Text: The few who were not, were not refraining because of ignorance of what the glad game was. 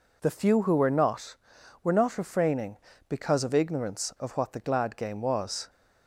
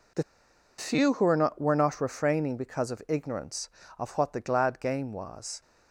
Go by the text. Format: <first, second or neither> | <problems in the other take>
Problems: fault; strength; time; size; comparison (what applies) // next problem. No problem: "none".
first | pauses between "The" and "few"; noticeable; at 0.2 s; 0.55 s long